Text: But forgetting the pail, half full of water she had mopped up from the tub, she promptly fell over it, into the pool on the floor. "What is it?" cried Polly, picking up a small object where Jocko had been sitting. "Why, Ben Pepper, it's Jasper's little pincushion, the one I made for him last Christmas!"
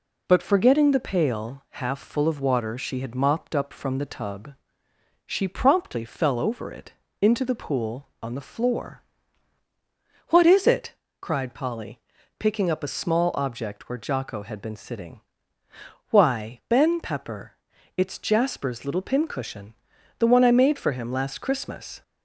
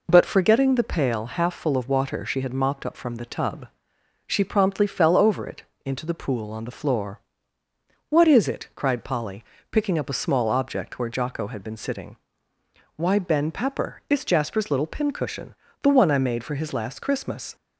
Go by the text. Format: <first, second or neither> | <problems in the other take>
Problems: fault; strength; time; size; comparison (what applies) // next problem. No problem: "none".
first | says "his" for "him"; at 16.5 s